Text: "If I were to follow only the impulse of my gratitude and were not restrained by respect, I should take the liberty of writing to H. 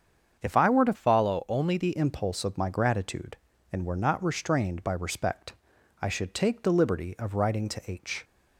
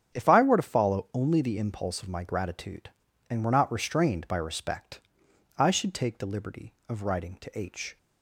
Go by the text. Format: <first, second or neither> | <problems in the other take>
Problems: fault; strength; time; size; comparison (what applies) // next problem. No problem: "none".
second | starts louder than the rest; strong; until 1.4 s; 7 dB; strong in the second // changes voice from "follow" to "the"; from 0.9 to 1.9 s; 1.0 s long